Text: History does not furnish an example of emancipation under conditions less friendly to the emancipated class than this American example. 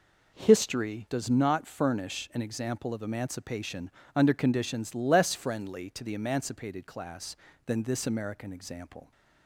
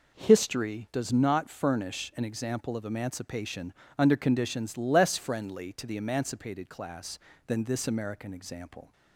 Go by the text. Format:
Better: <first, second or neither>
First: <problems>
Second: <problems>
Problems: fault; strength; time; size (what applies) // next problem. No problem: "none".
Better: neither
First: pauses between "emancipation" and "under"; slight; at 3.9 s; 0.24 s long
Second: pauses between "emancipation" and "under"; slight; at 3.7 s; 0.24 s long